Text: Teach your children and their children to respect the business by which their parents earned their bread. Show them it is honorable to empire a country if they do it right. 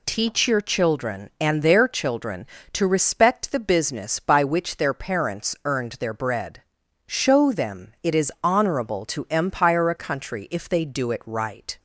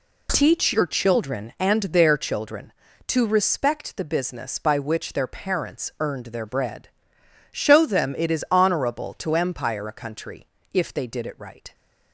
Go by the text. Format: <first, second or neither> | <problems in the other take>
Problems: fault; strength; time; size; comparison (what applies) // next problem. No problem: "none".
first | pauses between "country" and "if"; slight; at 10.4 s; 0.26 s long // says "did" for "do"; at 11.0 s